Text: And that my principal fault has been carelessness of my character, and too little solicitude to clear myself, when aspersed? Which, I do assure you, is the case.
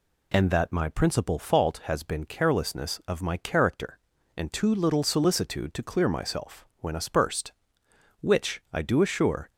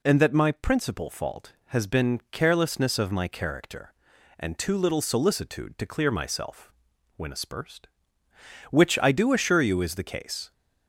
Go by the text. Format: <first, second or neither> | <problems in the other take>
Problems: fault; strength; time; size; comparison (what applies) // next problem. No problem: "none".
second | stops before "you is the case"; at 9.5 s